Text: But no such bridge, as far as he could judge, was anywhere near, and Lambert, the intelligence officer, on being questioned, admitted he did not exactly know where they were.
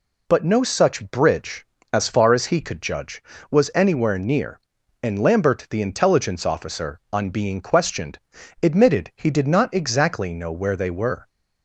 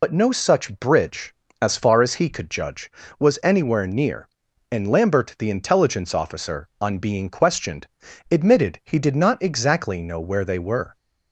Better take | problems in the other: first | loses the start of "But"; at 0.0 s; 65 ms

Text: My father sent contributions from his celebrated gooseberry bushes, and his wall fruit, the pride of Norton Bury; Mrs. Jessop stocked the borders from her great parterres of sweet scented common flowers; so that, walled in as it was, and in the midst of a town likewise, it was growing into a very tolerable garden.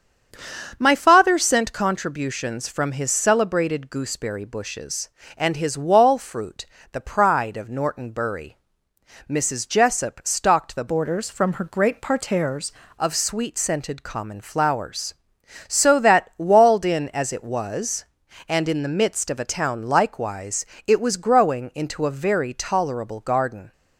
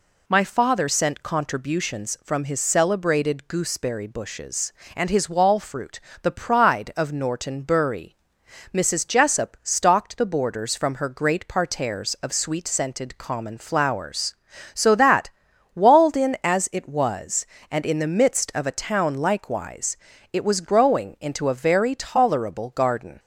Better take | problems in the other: second | starts louder than the rest; until 1.7 s; 7 dB // changes voice from "borders" to "parterres"; from 10.8 to 12.7 s; 1.9 s long

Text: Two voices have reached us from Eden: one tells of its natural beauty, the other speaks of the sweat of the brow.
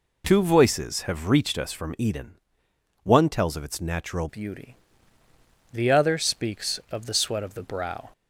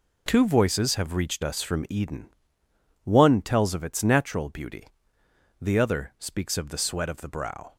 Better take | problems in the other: second | changes voice at "beauty"; from 4.2 s on; 3.8 s long

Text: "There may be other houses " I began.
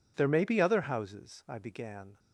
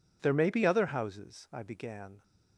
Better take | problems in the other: neither | none

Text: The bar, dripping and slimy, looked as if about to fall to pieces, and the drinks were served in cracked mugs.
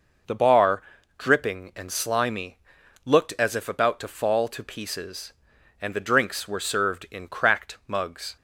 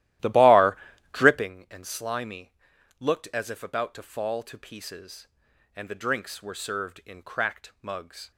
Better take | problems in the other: first | starts louder than the rest; strong; until 1.5 s; 14.5 dB

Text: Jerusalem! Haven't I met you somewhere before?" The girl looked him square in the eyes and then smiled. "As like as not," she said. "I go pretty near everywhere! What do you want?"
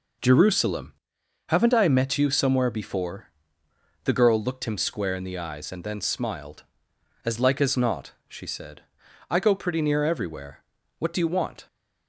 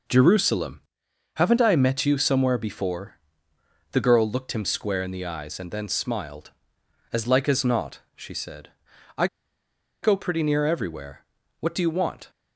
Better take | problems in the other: first | pauses between "I" and "go"; noticeable; at 9.2 s; 0.76 s long

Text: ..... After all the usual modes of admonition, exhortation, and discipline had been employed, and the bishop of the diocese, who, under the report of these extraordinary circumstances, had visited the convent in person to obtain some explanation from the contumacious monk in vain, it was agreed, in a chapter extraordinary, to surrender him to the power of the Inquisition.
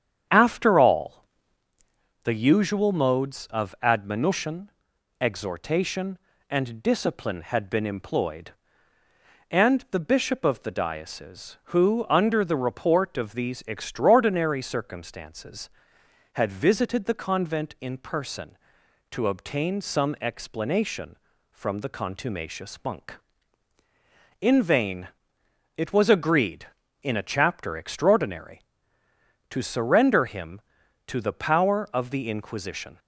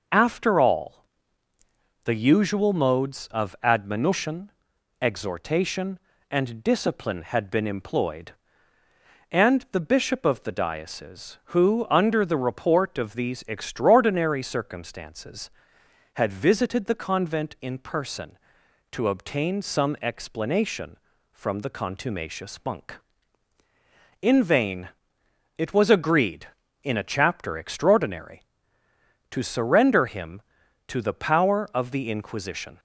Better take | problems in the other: second | starts louder than the rest; strong; until 1.7 s; 8.5 dB // pauses between "all" and "the"; at 1.2 s; 1.0 s long; also in the second

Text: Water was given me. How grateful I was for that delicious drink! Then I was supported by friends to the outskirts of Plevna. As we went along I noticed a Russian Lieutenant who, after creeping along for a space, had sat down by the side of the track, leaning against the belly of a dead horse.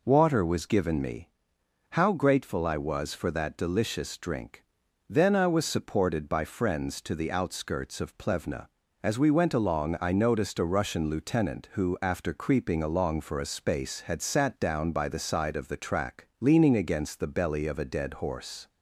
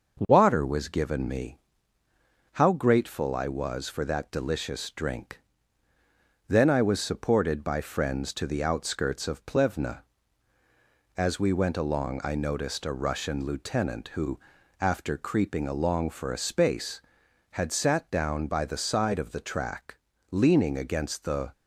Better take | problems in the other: first | starts louder than the rest; until 1.2 s; 6 dB // stops before "belly of a dead horse"; at 21.5 s

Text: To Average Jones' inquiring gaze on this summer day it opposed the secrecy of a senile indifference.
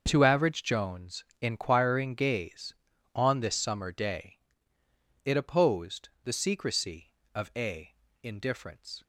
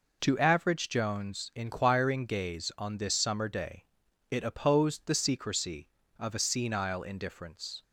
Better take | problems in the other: second | starts louder than the rest; until 1.0 s; 6.5 dB // pauses between "Jones" and "inquiring"; slight; at 1.2 s; 0.16 s long // pauses between "day" and "it"; noticeable; at 4.3 s; 0.88 s long; also in the second // pauses between "opposed" and "the"; slight; at 6.0 s; 0.16 s long // skips "senile"; at 8.0 s

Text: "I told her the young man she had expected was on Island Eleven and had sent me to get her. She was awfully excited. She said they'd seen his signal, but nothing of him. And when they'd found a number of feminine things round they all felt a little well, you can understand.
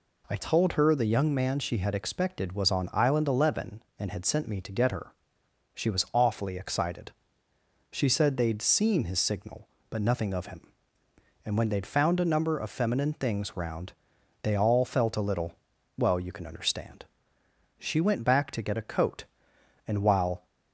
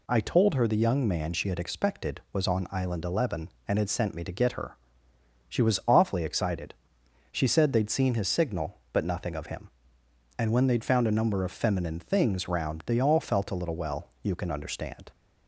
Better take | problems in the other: second | pauses between "round" and "they"; noticeable; at 13.9 s; 0.48 s long // pauses between "little" and "well"; at 15.5 s; 0.42 s long // goes on to say "She went back to get a coat and while"; strong; from 17.7 s on; 2.6 s long

